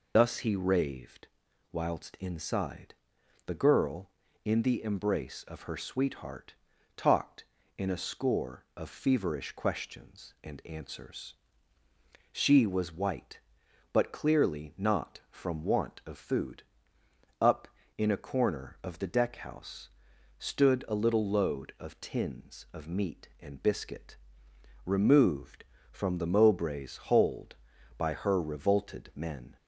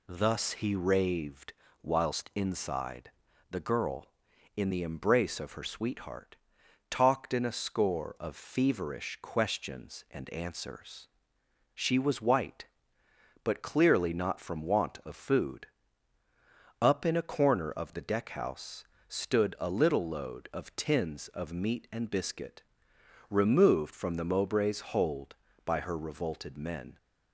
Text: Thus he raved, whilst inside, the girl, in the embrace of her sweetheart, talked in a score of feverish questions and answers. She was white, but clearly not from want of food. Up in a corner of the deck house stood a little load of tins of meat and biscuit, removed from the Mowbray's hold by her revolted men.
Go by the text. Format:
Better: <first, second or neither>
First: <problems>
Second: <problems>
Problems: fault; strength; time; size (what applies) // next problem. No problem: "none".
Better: second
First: loses the start of "Thus"; at 0.1 s; 55 ms // pauses between "house" and "stood"; noticeable; at 19.8 s; 0.50 s long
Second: pauses between "house" and "stood"; slight; at 18.8 s; 0.24 s long